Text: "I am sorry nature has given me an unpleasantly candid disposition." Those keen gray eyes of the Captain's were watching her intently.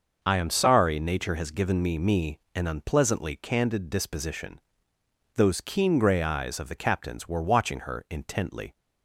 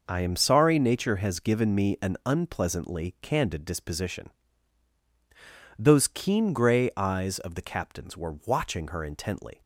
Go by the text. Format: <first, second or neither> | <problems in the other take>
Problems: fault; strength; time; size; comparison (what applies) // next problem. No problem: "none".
second | starts louder than the rest; until 1.2 s; 6 dB // says "me" twice; at 1.9 s